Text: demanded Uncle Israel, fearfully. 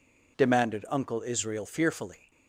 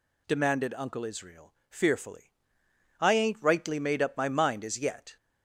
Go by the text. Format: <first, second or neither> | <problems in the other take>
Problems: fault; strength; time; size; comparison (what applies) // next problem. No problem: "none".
first | goes on to say "I ain't rightly made up my mind as yet"; strong; from 2.9 s on; 2.1 s long